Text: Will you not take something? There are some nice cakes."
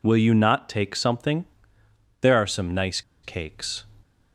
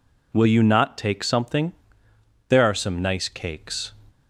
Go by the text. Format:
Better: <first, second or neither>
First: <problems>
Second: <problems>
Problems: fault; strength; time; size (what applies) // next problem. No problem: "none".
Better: second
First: pauses between "nice" and "cakes"; slight; at 3.0 s; 0.22 s long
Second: none